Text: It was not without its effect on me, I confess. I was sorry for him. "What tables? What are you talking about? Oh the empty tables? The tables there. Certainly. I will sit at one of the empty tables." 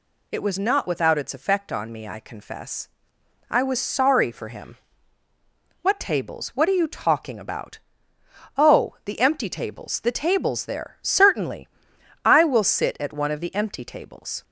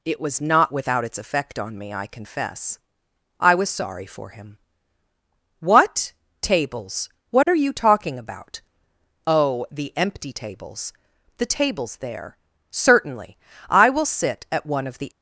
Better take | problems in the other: first | pauses between "What" and "tables"; slight; at 6.1 s; 0.28 s long // stops before "empty tables"; at 15.1 s

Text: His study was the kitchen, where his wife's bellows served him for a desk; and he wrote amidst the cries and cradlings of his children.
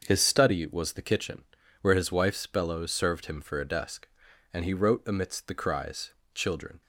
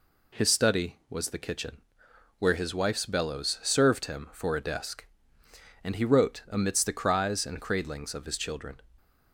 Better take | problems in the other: second | starts louder than the rest; until 1.0 s; 6.5 dB // skips "and cradlings of his"; at 6.2 s

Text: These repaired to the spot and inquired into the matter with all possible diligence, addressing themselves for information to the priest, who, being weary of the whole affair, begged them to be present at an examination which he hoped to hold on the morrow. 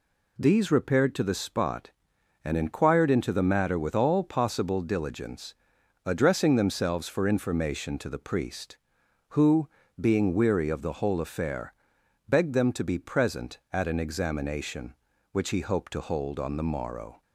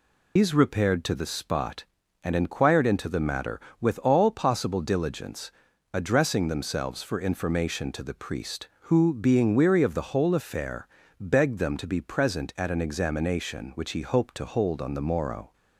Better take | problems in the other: first | loses the start of "These"; at 0.3 s; 120 ms

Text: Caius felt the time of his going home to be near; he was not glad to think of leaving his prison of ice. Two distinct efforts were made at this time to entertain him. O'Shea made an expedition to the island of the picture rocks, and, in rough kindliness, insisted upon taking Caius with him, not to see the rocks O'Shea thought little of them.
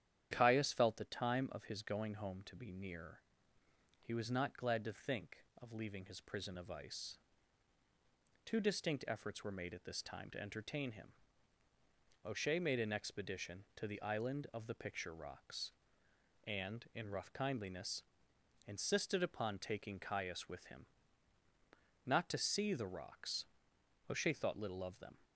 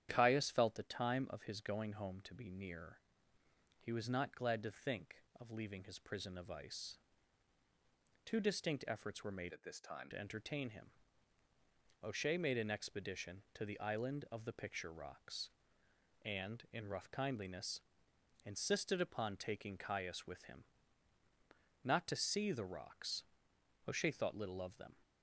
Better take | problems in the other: first | starts louder than the rest; strong; until 1.1 s; 10 dB; strong in the first // changes voice from "at" to "time"; from 9.5 to 10.0 s; 0.5 s long // pauses between "rocks" and "O'Shea"; noticeable; at 23.2 s; 0.62 s long; noticeable in the first

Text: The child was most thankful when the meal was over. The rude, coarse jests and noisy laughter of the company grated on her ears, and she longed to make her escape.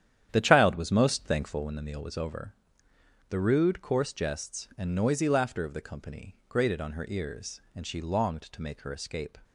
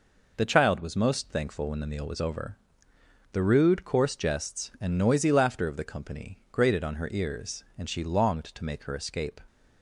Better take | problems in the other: second | starts louder than the rest; strong; until 1.7 s; 10 dB

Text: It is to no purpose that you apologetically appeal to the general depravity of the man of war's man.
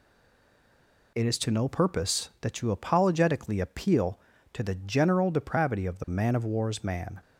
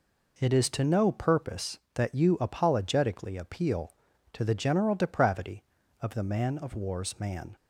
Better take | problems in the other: second | stays silent before the first word; until 1.1 s; 1.1 s long

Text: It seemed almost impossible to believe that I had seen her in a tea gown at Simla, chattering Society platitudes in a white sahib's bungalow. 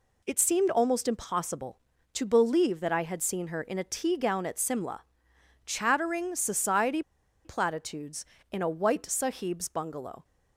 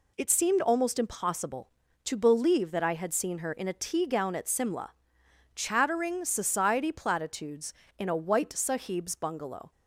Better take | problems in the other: second | pauses between "Society" and "platitudes"; at 7.0 s; 0.42 s long

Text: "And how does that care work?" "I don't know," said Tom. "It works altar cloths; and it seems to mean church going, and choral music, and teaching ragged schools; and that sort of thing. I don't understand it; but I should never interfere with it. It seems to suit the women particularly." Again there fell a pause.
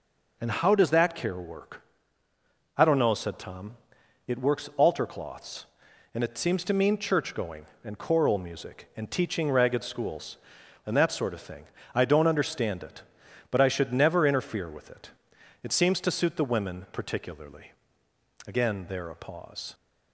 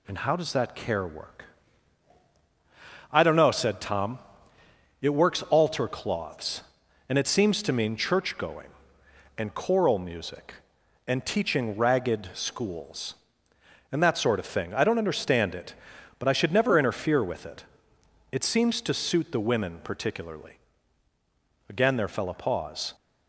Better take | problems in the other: second | skips "fell"; at 19.0 s

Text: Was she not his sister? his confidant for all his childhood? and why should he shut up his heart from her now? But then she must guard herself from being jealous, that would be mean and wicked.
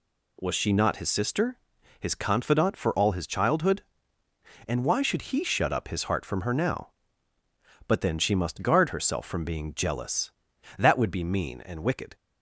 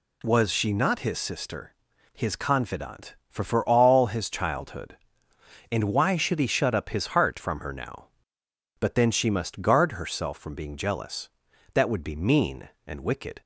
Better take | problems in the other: first | says "for" twice; at 3.4 s

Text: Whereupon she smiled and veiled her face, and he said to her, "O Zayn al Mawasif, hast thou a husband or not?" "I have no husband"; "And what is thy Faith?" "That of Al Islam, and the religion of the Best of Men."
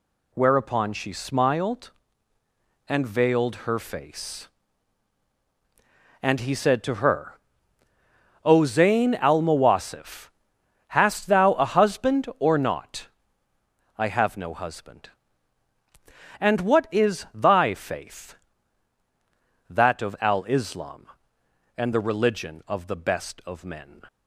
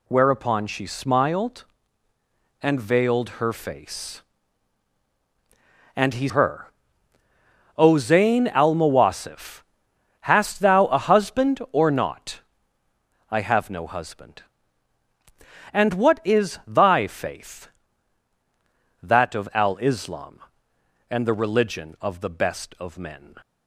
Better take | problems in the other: first | skips "said to"; at 6.2 s

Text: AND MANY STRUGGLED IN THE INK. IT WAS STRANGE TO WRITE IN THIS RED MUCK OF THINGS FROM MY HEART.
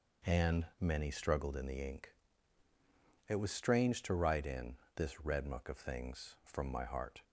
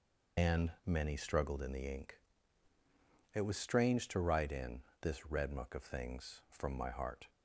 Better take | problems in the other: first | loses the start of "AND"; at 0.3 s; 95 ms // pauses between "IN" and "THIS"; slight; at 4.8 s; 0.18 s long; slight in the first

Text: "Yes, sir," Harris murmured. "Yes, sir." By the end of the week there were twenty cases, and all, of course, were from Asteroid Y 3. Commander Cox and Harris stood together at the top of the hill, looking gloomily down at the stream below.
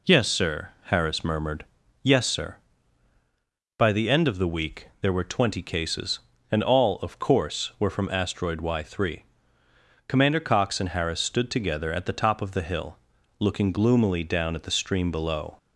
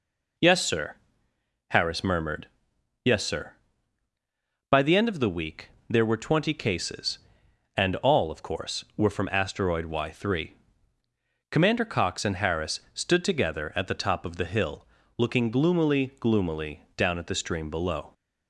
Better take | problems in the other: first | pauses between "week" and "there"; slight; at 5.6 s; 0.20 s long // says "gloomily" twice; at 16.1 s

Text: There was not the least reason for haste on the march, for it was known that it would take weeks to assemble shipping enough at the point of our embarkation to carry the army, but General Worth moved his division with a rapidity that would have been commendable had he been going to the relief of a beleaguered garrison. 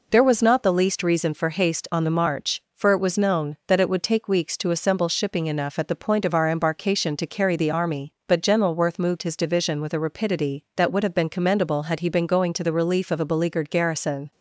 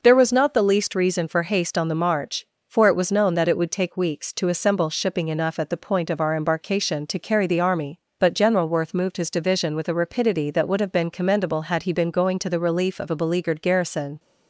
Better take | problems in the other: neither | none

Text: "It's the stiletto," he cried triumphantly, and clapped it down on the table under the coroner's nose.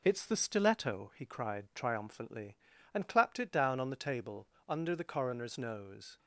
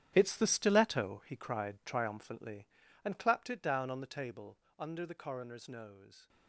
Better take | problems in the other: first | gets quieter; strong; throughout; 12.5 dB // pauses between "table" and "under"; slight; at 4.5 s; 0.22 s long; slight in the first

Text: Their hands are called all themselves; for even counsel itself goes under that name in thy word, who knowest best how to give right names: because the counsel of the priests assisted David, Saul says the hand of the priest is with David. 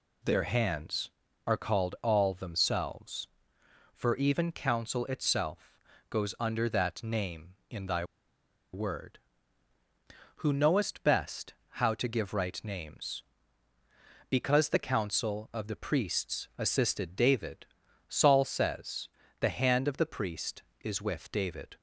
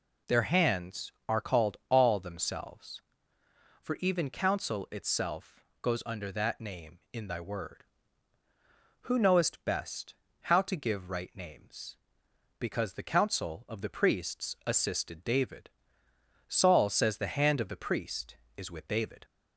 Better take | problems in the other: second | pauses between "itself" and "goes"; slight; at 5.7 s; 0.32 s long; slight in the second // pauses between "thy" and "word"; noticeable; at 8.0 s; 0.68 s long // pauses between "best" and "how"; slight; at 11.5 s; 0.20 s long; slight in the second // pauses between "says" and "the"; slight; at 19.0 s; 0.30 s long

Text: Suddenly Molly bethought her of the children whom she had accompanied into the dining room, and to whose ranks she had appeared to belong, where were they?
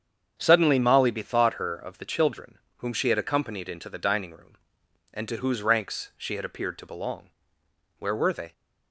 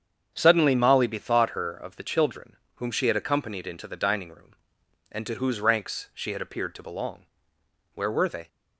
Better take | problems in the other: neither | starts louder than the rest; strong; the same in both // pauses between "children" and "whom"; slight; the same in both

